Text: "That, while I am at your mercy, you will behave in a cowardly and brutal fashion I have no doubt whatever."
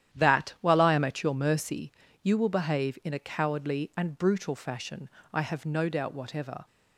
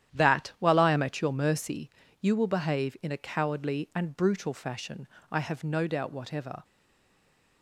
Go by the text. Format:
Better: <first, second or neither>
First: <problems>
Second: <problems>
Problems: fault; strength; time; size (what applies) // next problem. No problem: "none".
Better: first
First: starts louder than the rest; strong; until 1.1 s; 11 dB // pauses between "fashion" and "I"; slight; at 5.0 s; 0.24 s long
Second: starts louder than the rest; strong; until 1.1 s; 11 dB // pauses between "fashion" and "I"; slight; at 5.0 s; 0.24 s long // stays silent after the last word; from 6.6 s on; 1.0 s long